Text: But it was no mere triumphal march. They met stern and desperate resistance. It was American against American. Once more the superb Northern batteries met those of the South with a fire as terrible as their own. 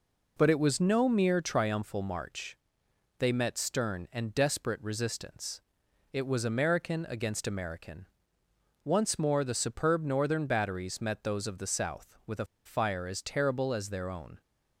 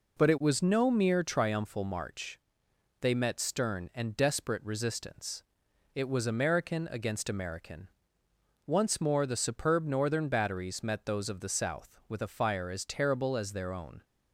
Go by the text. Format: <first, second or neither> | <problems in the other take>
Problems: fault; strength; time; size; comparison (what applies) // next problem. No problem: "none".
second | pauses between "a" and "fire"; slight; at 12.4 s; 0.19 s long